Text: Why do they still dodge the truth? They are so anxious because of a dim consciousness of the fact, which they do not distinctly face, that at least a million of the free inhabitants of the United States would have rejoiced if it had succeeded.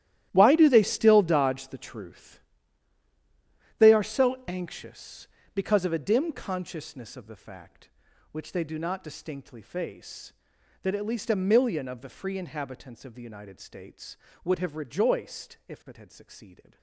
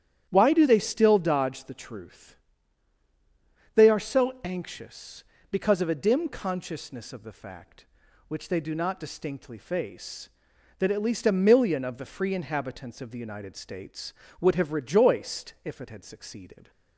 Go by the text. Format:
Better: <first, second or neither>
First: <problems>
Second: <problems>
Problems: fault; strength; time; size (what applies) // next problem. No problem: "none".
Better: second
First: gets quieter; strong; throughout; 14 dB // starts louder than the rest; strong; until 1.3 s; 12.5 dB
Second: starts louder than the rest; strong; until 1.3 s; 10 dB